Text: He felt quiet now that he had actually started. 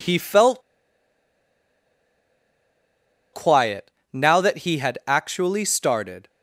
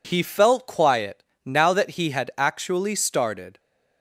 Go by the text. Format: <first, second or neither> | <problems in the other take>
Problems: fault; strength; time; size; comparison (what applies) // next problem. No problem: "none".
second | pauses between "felt" and "quiet"; strong; at 0.6 s; 2.7 s long // pauses between "quiet" and "now"; slight; at 3.9 s; 0.24 s long; slight in the second